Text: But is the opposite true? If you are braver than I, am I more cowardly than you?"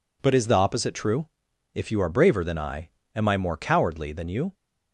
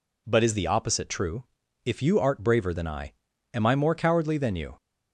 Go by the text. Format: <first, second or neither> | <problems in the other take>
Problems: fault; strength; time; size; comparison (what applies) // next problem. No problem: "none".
first | says "art" for "are"; at 2.1 s